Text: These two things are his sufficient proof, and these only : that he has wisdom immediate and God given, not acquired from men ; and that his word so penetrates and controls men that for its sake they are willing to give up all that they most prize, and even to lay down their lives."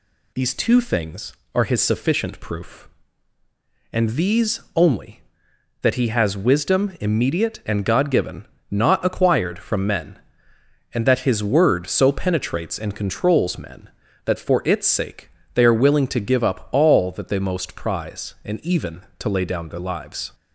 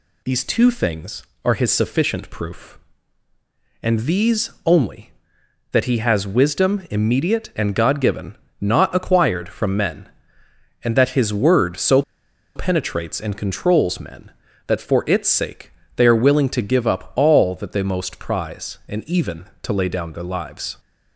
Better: first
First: pauses between "sake" and "they"; slight; at 15.3 s; 0.24 s long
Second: pauses between "so" and "penetrates"; noticeable; at 12.0 s; 0.54 s long // pauses between "sake" and "they"; slight; at 15.7 s; 0.24 s long

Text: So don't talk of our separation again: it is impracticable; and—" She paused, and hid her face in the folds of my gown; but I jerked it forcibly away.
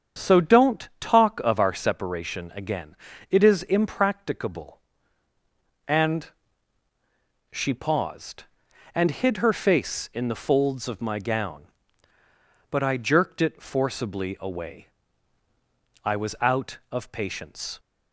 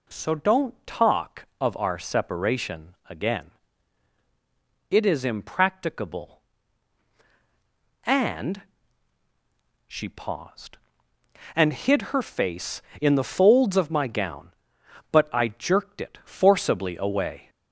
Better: second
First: starts louder than the rest; strong; until 1.2 s; 7.5 dB // goes on to say "I was out of patience"; strong; from 16.0 s on; 1.7 s long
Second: none

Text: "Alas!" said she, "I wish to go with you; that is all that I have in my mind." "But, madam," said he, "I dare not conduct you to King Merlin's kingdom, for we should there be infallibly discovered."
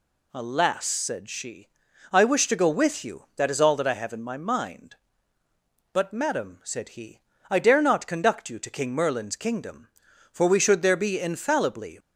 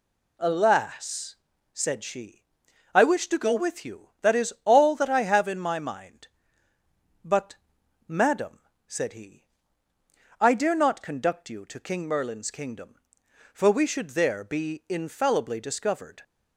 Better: second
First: stops before "discovered"; at 11.9 s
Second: none

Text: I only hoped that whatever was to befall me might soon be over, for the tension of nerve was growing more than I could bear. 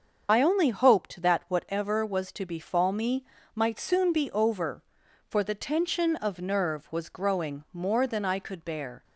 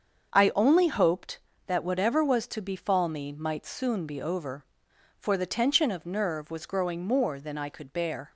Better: second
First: loses the start of "I"; at 0.2 s; 40 ms // starts louder than the rest; until 1.3 s; 6.5 dB // pauses between "me" and "might"; slight; at 3.2 s; 0.30 s long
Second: starts louder than the rest; until 1.7 s; 6.5 dB

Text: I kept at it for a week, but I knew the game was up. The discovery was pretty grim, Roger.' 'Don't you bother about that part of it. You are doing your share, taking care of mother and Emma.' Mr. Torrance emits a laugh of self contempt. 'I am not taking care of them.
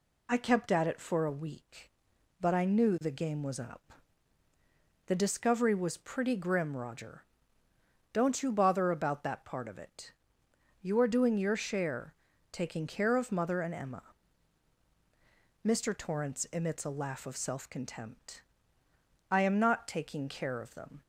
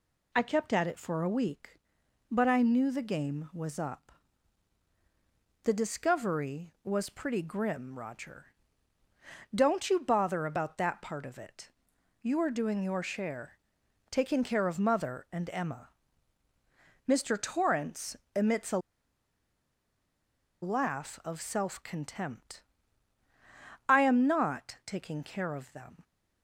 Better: first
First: none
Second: pauses between "Torrance" and "emits"; slight; at 18.1 s; 0.18 s long // pauses between "a" and "laugh"; strong; at 18.7 s; 1.8 s long

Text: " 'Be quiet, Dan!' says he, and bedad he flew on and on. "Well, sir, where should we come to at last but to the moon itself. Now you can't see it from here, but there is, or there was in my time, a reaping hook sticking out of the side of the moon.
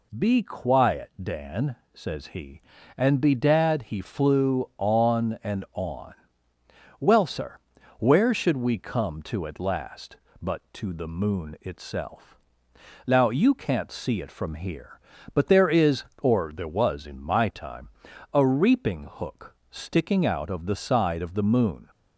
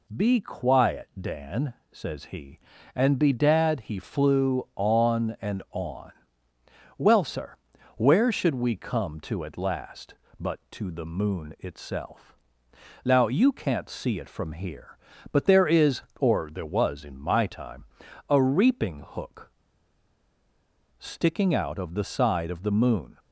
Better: first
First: none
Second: pauses between "hook" and "sticking"; strong; at 19.5 s; 1.4 s long

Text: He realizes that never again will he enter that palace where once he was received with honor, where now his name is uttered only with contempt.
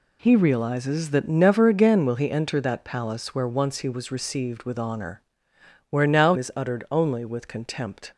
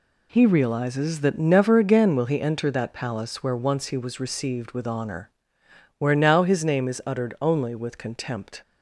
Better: second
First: skips "his name"; at 6.3 s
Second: none

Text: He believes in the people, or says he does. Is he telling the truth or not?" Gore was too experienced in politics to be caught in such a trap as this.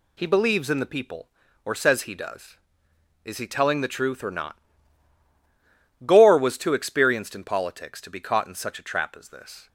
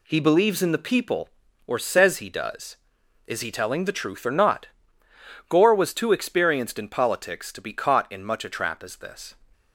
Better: first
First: none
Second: says "much" for "such"; at 8.2 s

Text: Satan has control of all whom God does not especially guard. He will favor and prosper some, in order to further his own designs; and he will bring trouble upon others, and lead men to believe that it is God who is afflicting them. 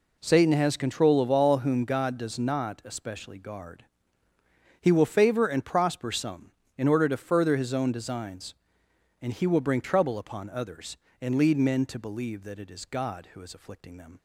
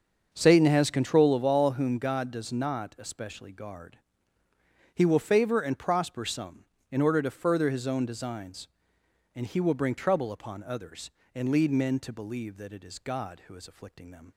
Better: first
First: none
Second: starts louder than the rest; until 1.4 s; 6.5 dB

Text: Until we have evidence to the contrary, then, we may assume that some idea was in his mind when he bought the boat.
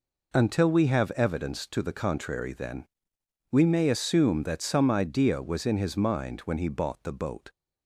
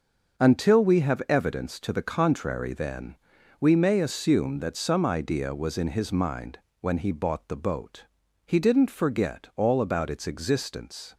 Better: first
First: none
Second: starts louder than the rest; until 1.4 s; 6.5 dB // pauses between "mind" and "when"; slight; at 6.5 s; 0.22 s long // goes on to say "He didn't forget all about its existence"; strong; from 8.4 s on; 2.7 s long

